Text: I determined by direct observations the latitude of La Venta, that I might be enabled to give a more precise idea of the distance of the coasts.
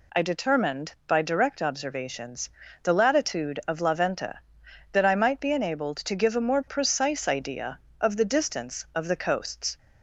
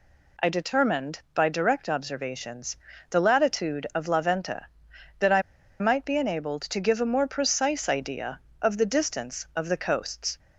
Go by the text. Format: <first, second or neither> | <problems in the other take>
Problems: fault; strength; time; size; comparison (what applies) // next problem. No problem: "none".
first | pauses between "observations" and "the"; slight; at 2.7 s; 0.36 s long; slight in the first // pauses between "I" and "might"; at 5.4 s; 0.38 s long